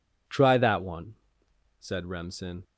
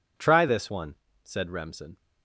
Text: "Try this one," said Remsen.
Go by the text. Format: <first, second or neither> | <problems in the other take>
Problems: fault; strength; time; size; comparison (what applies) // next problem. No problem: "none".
second | says "that" for "this"; at 0.5 s